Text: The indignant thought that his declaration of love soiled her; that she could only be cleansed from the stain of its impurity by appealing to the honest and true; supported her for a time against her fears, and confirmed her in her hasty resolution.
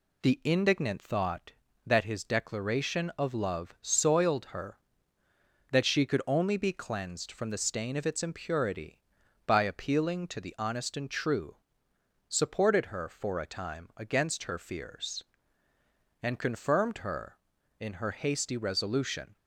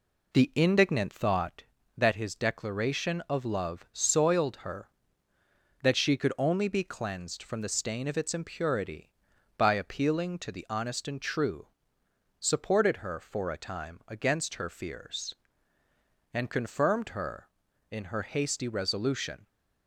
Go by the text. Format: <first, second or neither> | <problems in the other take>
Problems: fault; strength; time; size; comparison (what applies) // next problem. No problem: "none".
first | starts louder than the rest; slight; until 1.7 s; 3 dB